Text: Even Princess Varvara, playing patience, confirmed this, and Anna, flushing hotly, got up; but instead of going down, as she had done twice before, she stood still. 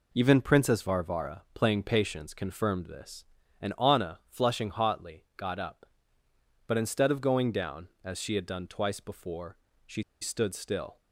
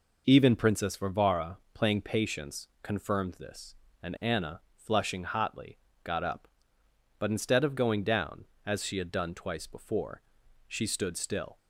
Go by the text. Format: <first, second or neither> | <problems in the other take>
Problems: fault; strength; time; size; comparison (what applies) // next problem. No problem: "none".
second | pauses between "she" and "stood"; slight; at 10.0 s; 0.18 s long